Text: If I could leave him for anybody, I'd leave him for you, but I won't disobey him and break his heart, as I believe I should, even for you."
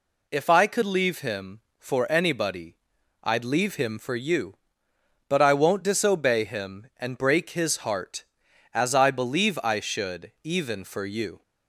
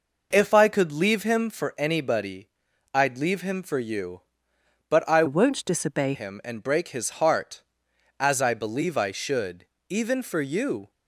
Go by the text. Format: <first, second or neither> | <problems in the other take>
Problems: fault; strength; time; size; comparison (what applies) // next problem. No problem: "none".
first | changes voice from "won't" to "disobey"; from 5.2 to 6.1 s; 0.9 s long